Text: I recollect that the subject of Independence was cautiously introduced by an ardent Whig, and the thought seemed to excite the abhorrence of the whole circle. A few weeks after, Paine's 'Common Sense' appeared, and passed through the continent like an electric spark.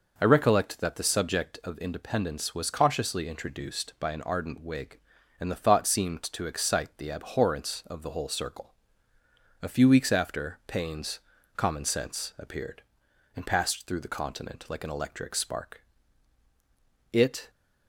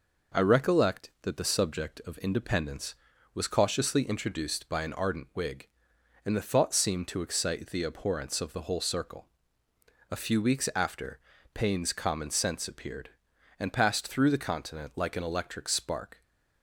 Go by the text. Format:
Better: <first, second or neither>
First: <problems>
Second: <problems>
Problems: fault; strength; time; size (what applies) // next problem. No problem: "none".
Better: second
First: pauses between "Paine's" and "Common"; at 11.1 s; 0.38 s long // goes on to say "It"; slight; from 17.1 s on; 0.38 s long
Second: none